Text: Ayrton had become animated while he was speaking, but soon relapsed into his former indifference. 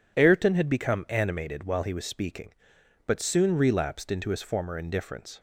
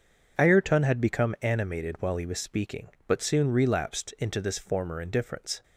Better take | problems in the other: first | says "this" for "his"; at 4.3 s

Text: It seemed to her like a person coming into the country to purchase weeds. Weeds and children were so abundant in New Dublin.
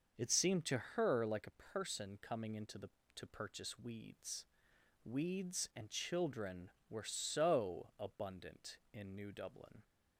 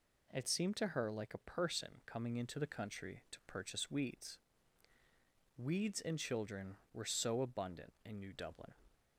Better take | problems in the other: second | starts louder than the rest; noticeable; until 1.2 s; 6 dB // skips "country"; at 3.0 s

